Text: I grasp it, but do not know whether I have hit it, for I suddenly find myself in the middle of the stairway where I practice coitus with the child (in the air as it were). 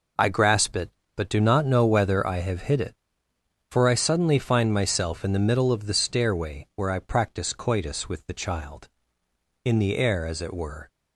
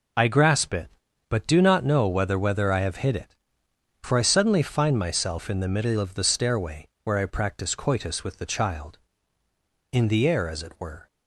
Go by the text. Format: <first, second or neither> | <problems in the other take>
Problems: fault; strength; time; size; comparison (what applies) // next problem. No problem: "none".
first | says "whether" twice; at 2.3 s // pauses between "stairway" and "where"; slight; at 6.8 s; 0.16 s long